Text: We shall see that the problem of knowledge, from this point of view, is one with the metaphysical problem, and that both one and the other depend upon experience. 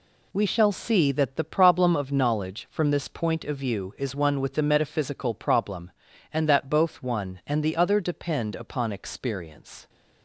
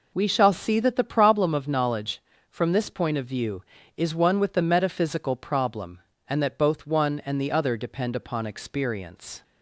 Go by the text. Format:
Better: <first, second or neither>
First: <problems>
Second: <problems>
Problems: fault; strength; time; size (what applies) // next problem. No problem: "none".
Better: neither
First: none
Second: none